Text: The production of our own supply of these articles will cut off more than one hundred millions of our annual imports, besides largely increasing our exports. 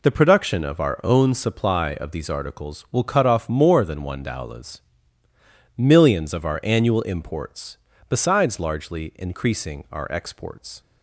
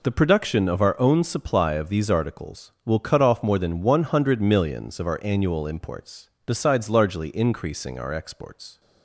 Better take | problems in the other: second | says "dowlas" for "hundred"; at 4.2 s

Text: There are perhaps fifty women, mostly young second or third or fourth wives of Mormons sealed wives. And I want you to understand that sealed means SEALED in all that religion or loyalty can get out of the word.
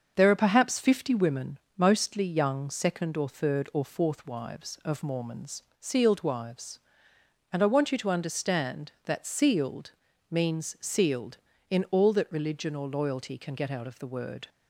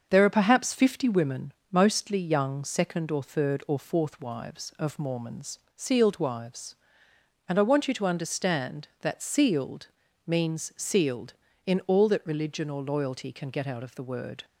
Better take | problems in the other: neither | starts louder than the rest; the same in both // pauses between "Mormons" and "sealed"; slight; the same in both // pauses between "sealed" and "means"; slight; the same in both

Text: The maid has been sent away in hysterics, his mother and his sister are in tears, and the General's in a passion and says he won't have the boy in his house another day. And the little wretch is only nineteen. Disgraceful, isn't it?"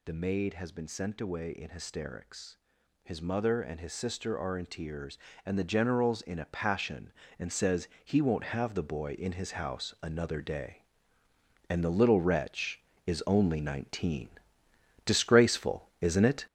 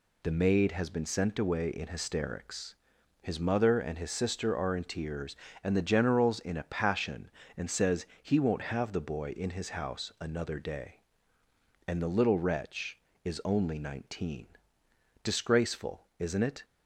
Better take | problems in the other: second | gets louder; throughout; 6.5 dB // pauses between "says" and "he"; slight; at 7.8 s; 0.18 s long; slight in the second

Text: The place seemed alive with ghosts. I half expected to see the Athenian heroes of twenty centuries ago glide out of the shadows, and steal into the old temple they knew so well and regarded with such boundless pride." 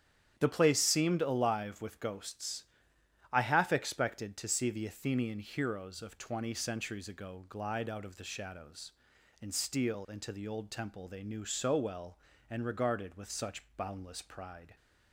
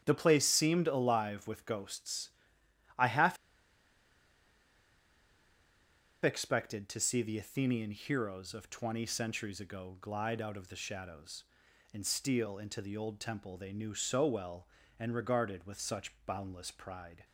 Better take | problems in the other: first | starts louder than the rest; strong; until 1.0 s; 9.5 dB; strong in the first // pauses between "half" and "expected"; strong; at 3.3 s; 2.8 s long

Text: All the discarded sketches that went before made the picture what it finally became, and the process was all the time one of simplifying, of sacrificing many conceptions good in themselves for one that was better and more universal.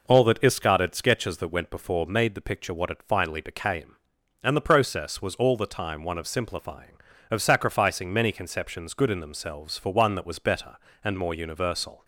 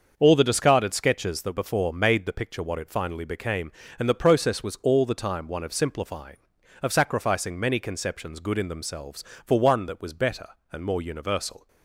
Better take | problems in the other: first | starts louder than the rest; until 1.1 s; 6.5 dB // skips "went"; at 1.5 s

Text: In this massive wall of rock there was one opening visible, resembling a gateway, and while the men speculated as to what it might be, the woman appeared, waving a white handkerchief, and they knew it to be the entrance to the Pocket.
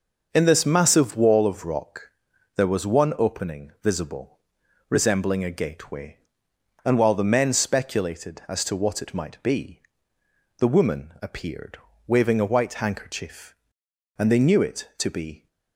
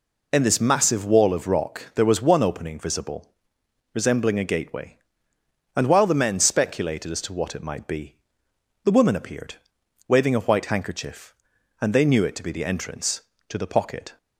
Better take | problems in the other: second | pauses between "rock" and "there"; at 2.1 s; 0.44 s long // stops before "the entrance to the Pocket"; at 15.4 s

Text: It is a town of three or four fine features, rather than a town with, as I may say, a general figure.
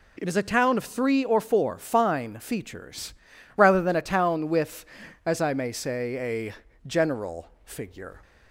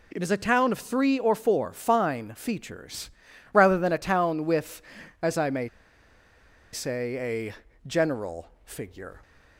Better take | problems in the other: first | pauses between "may" and "say"; at 5.6 s; 1.0 s long // pauses between "general" and "figure"; slight; at 8.4 s; 0.16 s long; slight in the first

